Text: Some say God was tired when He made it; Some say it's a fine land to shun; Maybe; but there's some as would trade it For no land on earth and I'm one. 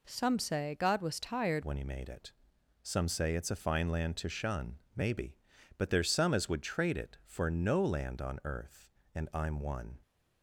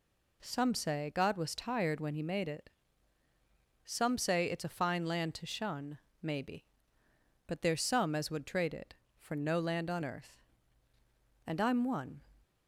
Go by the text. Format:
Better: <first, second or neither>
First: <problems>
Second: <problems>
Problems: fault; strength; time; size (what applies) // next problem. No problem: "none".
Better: second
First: changes voice at "when"; from 1.6 s on; 8.3 s long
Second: none